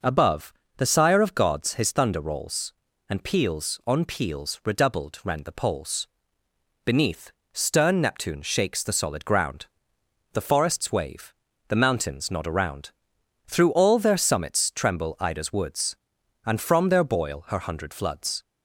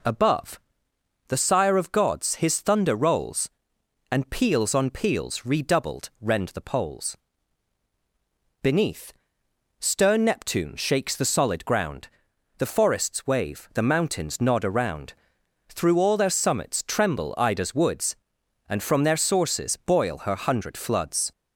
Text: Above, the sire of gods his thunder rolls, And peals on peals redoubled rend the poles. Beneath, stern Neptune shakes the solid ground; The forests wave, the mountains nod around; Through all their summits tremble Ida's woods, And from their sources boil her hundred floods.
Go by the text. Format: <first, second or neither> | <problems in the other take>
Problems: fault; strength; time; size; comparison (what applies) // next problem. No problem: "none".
second | skips "sources"; at 17.0 s